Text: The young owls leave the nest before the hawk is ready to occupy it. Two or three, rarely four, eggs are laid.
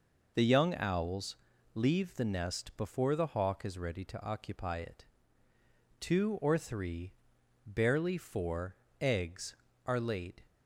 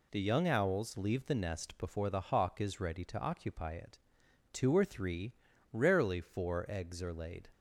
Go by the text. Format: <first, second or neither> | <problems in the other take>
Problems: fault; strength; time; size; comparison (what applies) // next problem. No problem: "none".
second | pauses between "owls" and "leave"; at 1.3 s; 0.38 s long // says "barely" for "rarely"; at 7.6 s